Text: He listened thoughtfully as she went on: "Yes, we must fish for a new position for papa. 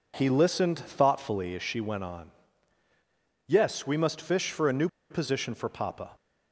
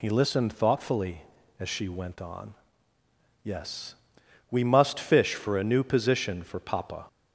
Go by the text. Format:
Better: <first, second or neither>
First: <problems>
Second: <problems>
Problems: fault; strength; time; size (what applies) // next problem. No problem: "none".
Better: second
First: pauses between "new" and "position"; slight; at 4.8 s; 0.23 s long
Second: none